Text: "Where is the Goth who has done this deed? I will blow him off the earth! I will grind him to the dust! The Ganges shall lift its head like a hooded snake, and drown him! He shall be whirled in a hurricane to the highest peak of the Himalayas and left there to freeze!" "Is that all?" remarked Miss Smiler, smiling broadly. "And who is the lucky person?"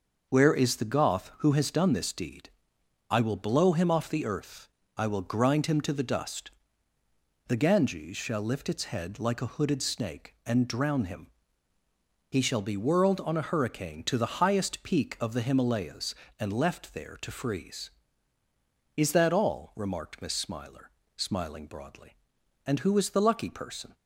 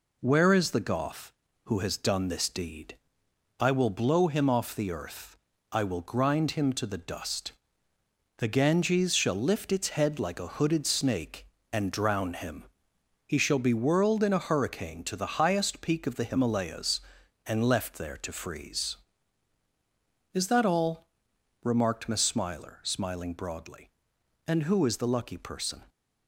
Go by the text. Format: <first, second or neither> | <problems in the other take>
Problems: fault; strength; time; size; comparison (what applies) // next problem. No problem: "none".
second | starts louder than the rest; noticeable; until 1.3 s; 6 dB // says "on" for "in"; at 13.2 s